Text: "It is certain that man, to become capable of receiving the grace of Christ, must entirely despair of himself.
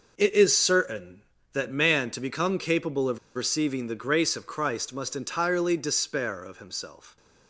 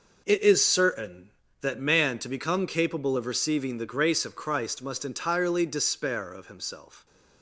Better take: second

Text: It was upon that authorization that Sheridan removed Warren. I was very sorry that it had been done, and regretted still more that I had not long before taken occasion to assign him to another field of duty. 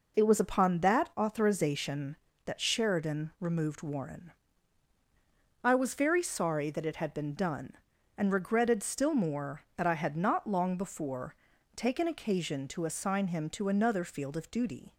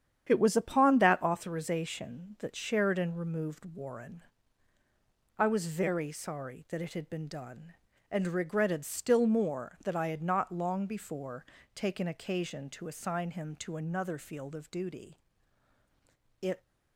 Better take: first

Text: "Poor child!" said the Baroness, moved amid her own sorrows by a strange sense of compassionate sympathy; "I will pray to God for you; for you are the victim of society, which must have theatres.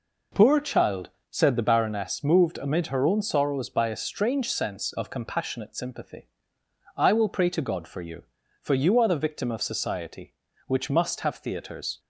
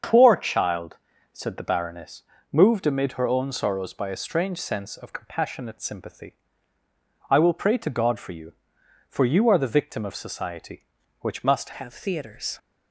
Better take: first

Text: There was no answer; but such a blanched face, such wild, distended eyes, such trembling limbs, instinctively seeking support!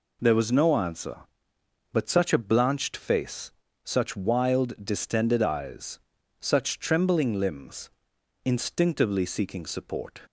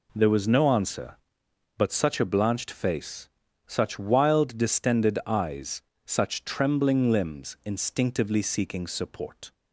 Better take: neither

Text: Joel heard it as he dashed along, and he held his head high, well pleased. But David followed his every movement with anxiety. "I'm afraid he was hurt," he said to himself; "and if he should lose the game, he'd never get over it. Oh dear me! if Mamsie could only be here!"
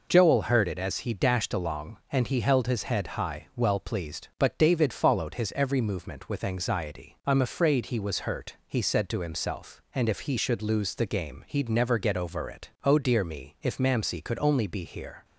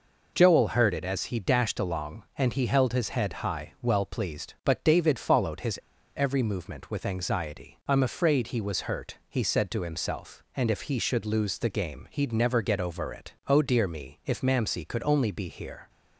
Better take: first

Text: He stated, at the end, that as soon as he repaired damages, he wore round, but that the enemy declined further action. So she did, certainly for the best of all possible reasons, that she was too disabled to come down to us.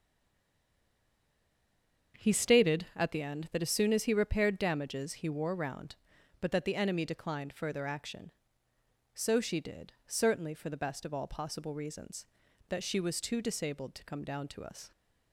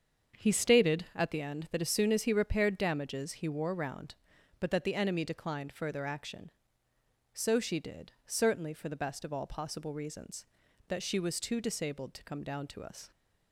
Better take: second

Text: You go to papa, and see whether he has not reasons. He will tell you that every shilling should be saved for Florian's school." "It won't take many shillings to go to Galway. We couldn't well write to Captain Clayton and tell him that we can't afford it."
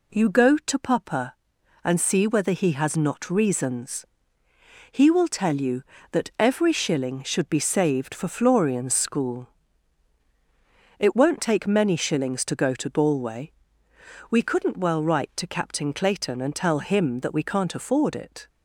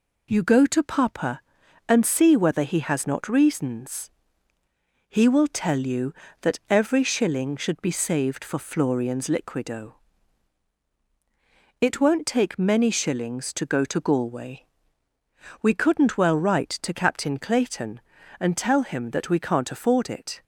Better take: first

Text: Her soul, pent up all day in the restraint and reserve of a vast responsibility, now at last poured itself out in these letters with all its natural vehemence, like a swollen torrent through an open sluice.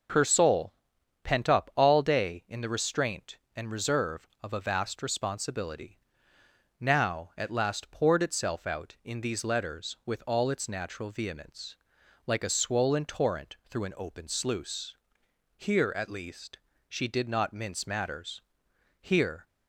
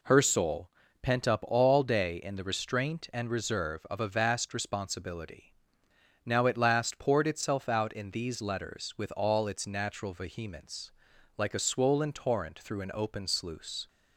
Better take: second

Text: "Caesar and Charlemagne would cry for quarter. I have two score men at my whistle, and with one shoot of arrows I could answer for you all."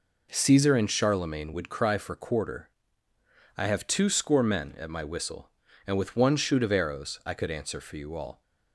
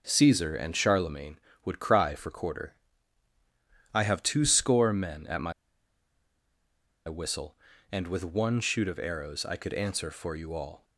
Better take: first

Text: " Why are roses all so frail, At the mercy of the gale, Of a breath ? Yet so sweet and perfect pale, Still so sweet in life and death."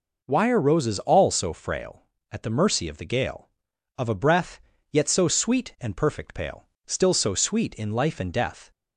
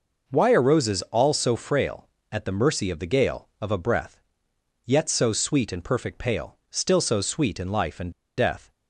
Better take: first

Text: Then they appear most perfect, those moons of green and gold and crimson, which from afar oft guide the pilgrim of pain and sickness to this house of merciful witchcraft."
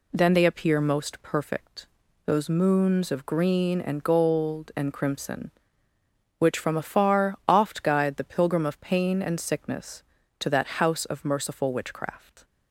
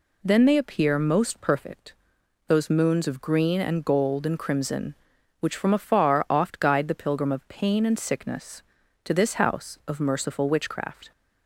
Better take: second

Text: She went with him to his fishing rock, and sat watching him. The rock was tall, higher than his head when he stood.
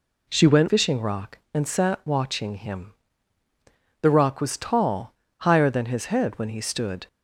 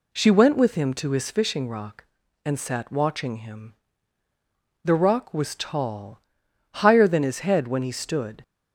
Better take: second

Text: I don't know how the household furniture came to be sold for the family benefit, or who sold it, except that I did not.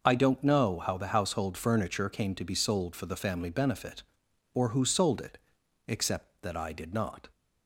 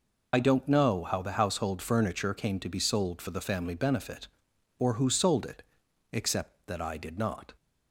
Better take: first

